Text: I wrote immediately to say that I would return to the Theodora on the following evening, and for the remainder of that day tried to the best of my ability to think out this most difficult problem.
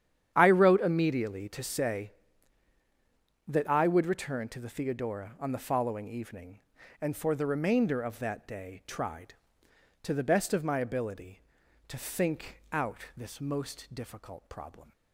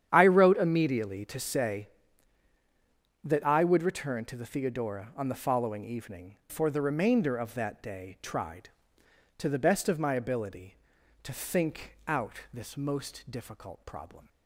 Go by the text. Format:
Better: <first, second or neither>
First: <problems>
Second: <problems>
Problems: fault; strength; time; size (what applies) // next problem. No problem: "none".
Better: first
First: starts louder than the rest; strong; until 1.3 s; 9 dB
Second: starts louder than the rest; strong; until 1.1 s; 9 dB // skips "and"; at 6.4 s